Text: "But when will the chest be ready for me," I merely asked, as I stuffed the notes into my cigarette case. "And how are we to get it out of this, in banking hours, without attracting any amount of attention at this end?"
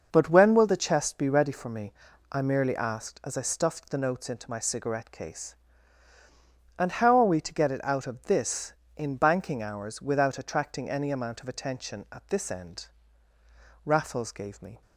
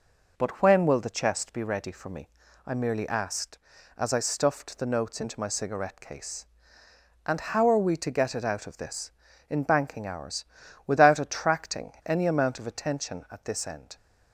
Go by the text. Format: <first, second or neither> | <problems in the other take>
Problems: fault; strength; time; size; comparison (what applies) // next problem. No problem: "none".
second | starts louder than the rest; until 1.1 s; 6.5 dB // goes on to say "Raffles gave me"; noticeable; from 13.8 s on; 0.96 s long